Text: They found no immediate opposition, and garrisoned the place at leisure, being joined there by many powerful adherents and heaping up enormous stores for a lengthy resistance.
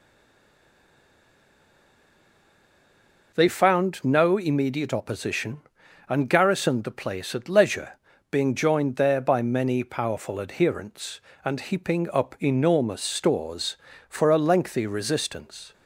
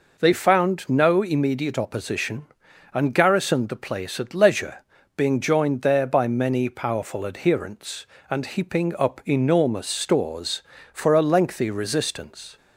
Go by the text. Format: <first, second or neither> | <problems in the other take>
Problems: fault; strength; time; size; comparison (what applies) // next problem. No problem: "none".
second | stays silent before the first word; strong; until 3.3 s; 3.3 s long